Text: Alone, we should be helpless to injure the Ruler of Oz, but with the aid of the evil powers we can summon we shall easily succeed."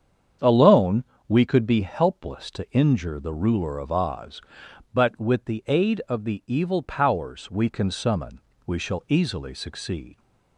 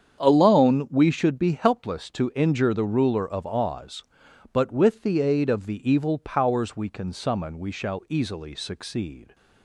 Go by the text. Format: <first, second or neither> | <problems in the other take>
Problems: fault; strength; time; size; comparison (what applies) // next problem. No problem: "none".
second | starts louder than the rest; strong; until 1.6 s; 8 dB; strong in the second // says "could" for "should"; at 1.4 s // pauses between "summon" and "we"; slight; at 8.3 s; 0.26 s long